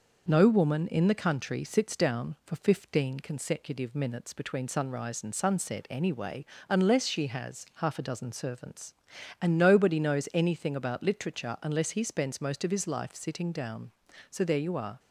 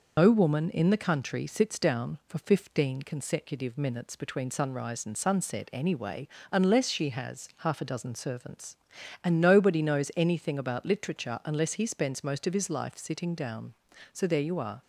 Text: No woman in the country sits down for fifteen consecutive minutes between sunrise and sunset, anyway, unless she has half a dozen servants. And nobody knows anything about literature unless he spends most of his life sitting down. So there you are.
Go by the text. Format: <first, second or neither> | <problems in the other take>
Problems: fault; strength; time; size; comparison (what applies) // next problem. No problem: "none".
first | loses the start of "No"; at 0.1 s; 85 ms